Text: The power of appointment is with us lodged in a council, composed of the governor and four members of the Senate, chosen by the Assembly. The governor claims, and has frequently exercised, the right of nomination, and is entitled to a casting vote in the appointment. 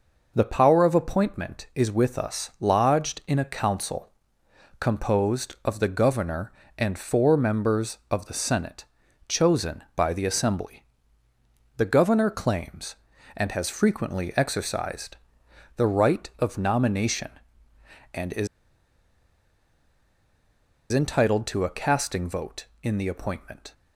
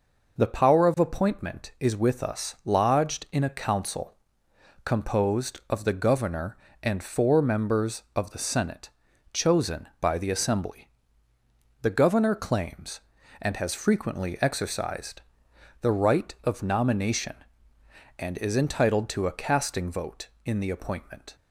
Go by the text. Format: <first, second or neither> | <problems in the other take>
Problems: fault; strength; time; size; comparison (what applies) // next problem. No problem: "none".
second | pauses between "is" and "entitled"; strong; at 18.4 s; 2.4 s long